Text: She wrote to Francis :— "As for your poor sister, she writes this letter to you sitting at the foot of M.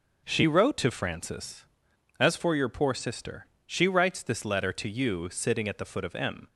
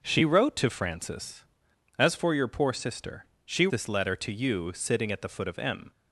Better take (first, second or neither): first